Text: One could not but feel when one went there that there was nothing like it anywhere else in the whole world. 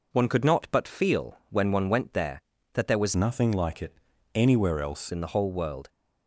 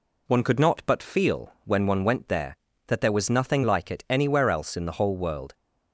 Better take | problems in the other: second | changes voice from "nothing" to "else"; from 3.1 to 5.0 s; 1.9 s long // pauses between "it" and "anywhere"; at 3.9 s; 0.38 s long

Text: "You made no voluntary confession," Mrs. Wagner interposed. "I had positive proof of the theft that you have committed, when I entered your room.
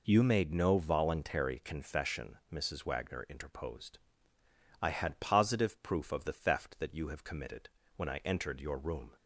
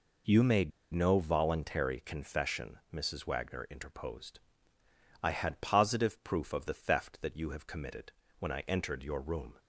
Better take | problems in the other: first | pauses between "made" and "no"; slight; at 0.7 s; 0.23 s long

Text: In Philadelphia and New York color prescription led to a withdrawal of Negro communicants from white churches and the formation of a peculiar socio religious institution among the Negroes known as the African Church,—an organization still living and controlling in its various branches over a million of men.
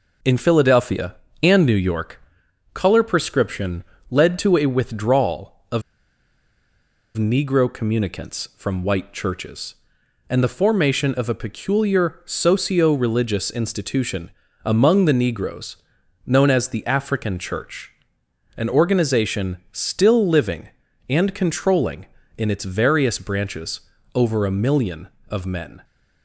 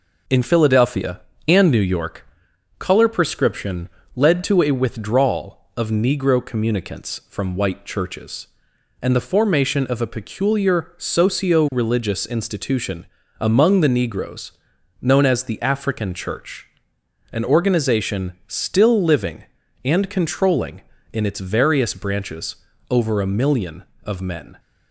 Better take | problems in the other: second | pauses between "York" and "color"; noticeable; at 2.2 s; 0.54 s long; noticeable in the second // pauses between "prescription" and "led"; slight; at 3.8 s; 0.28 s long; slight in the second // pauses between "of" and "Negro"; strong; at 5.8 s; 1.3 s long // pauses between "institution" and "among"; slight; at 14.3 s; 0.32 s long; slight in the second // pauses between "Negroes" and "known"; noticeable; at 15.7 s; 0.50 s long; noticeable in the second // pauses between "branches" and "over"; slight; at 23.8 s; 0.34 s long; slight in the second

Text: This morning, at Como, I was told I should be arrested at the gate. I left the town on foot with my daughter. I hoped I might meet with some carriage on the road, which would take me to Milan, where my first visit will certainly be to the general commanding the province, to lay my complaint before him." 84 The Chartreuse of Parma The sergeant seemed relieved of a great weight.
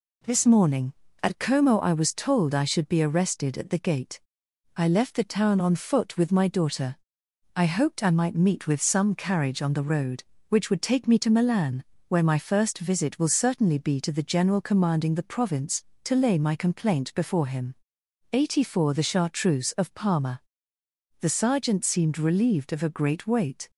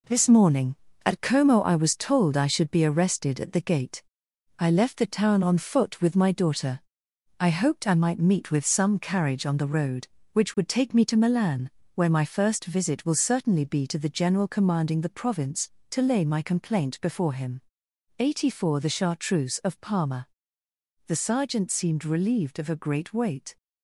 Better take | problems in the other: first | gets quieter; noticeable; throughout; 6 dB // pauses between "Parma" and "The"; noticeable; at 20.2 s; 0.80 s long; noticeable in the first

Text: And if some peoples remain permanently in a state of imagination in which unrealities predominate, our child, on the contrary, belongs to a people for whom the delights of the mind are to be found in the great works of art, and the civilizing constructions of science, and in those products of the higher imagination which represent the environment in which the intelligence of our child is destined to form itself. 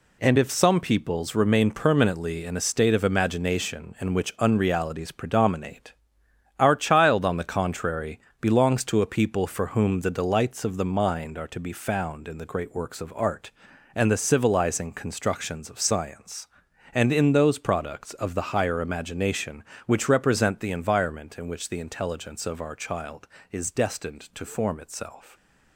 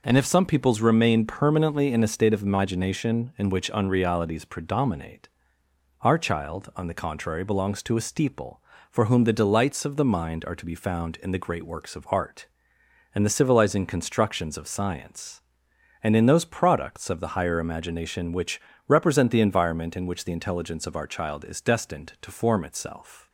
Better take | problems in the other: first | says "steeple" for "people"; at 8.0 s // pauses between "which" and "represent"; slight; at 18.5 s; 0.30 s long

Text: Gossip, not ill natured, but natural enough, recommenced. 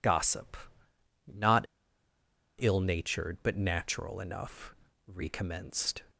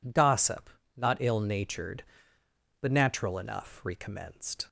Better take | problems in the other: second | pauses between "not" and "ill"; noticeable; at 1.6 s; 0.95 s long

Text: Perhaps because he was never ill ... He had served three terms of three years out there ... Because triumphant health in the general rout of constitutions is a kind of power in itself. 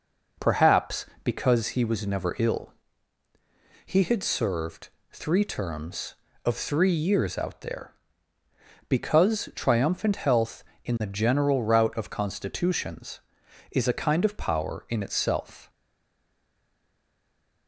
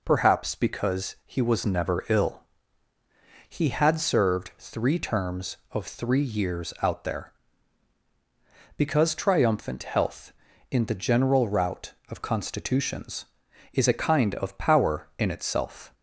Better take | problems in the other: second | pauses between "served" and "three"; slight; at 4.8 s; 0.22 s long // stays silent after the last word; noticeable; from 15.6 s on; 2.0 s long

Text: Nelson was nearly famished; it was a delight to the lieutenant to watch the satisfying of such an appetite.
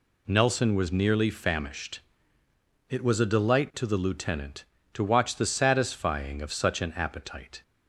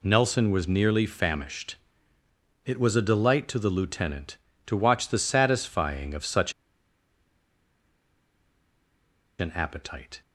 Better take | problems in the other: first | pauses between "such" and "an"; strong; at 6.5 s; 2.8 s long

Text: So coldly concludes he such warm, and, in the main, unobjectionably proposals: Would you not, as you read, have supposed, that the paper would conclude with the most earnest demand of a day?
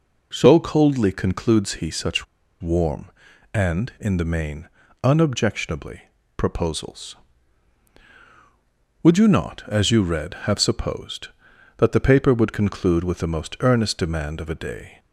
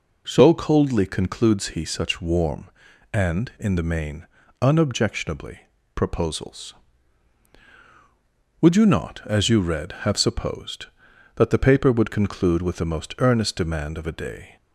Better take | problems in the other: second | pauses between "such" and "warm"; slight; at 2.2 s; 0.35 s long // pauses between "unobjectionably" and "proposals"; slight; at 6.0 s; 0.34 s long; slight in the second

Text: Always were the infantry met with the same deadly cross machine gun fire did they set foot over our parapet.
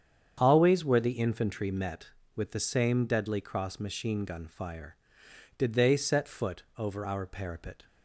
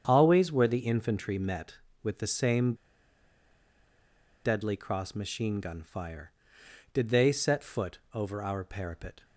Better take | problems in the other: first | starts louder than the rest; strong; until 1.0 s; 8 dB; strong in the first // pauses between "same" and "deadly"; strong; at 2.7 s; 1.7 s long // pauses between "foot" and "over"; slight; at 7.9 s; 0.16 s long; slight in the first

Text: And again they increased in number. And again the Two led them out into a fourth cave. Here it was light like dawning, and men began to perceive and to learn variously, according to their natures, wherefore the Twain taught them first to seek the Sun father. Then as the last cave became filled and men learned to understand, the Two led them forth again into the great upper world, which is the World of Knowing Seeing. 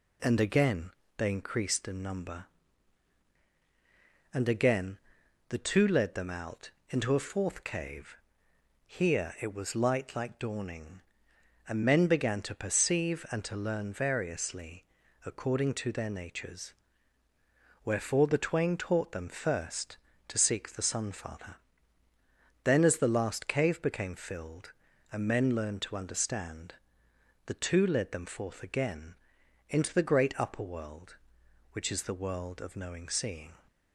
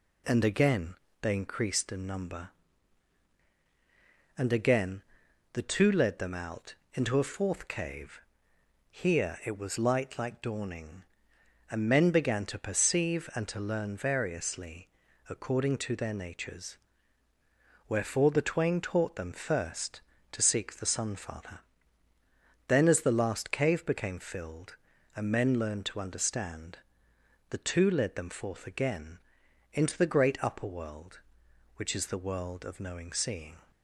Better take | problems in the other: neither | pauses between "again" and "they"; slight; the same in both // pauses between "again" and "the"; noticeable; the same in both // pauses between "out" and "into"; slight; the same in both // pauses between "again" and "into"; noticeable; the same in both

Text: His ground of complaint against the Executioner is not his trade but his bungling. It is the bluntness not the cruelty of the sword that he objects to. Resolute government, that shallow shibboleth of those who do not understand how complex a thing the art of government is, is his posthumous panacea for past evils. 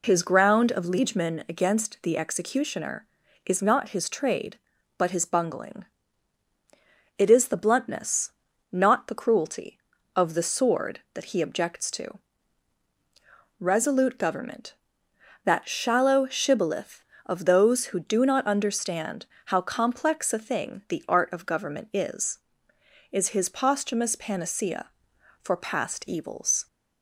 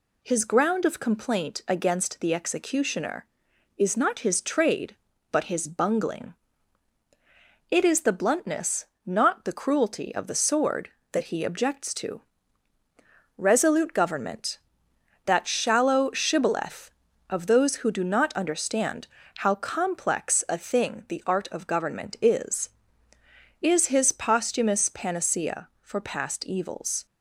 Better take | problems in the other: second | says "liegemen" for "complaint"; at 0.8 s // pauses between "bluntness" and "not"; at 8.3 s; 0.40 s long; slight in the second // pauses between "understand" and "how"; slight; at 19.2 s; 0.22 s long; slight in the second

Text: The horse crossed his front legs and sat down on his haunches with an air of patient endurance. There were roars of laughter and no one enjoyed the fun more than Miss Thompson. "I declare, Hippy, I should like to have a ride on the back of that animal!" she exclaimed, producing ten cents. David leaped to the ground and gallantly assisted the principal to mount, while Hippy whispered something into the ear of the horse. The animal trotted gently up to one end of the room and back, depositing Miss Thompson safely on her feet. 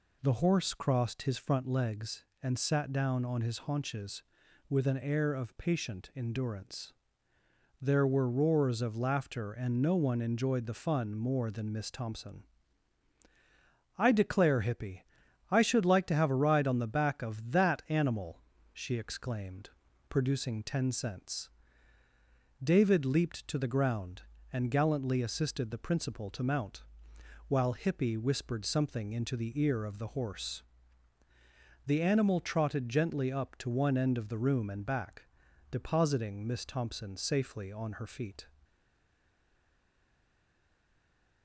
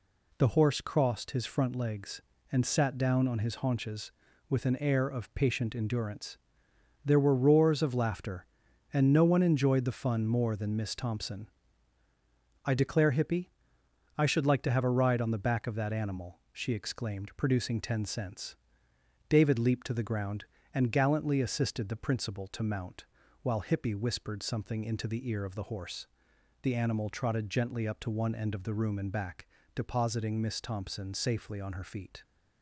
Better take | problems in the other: second | stays silent after the last word; strong; from 38.6 s on; 2.8 s long

